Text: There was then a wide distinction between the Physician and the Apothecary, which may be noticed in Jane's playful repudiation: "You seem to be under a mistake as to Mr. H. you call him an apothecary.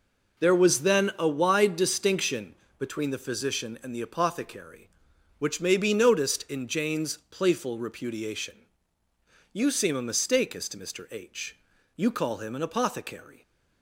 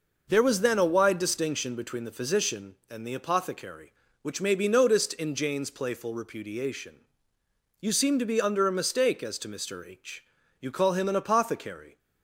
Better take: second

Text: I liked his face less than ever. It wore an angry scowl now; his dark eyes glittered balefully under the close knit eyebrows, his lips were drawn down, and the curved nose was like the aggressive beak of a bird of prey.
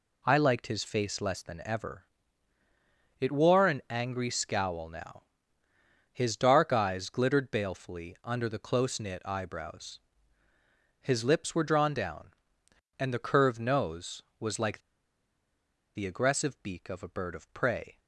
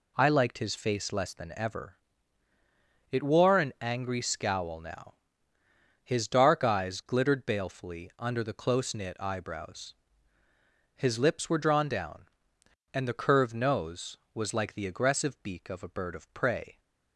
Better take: second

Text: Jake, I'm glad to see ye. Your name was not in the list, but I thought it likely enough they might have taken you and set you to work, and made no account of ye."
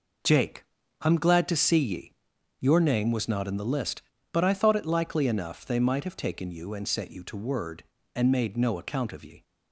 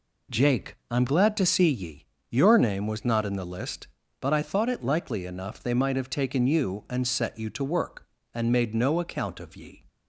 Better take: second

